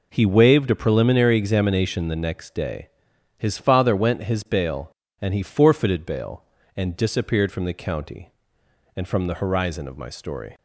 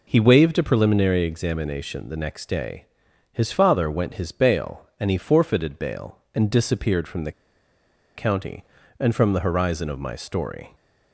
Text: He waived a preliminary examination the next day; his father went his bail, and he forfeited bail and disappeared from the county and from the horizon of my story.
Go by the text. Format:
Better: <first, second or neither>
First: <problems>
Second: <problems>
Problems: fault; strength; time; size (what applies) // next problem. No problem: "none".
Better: first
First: none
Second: pauses between "the" and "county"; noticeable; at 7.3 s; 0.83 s long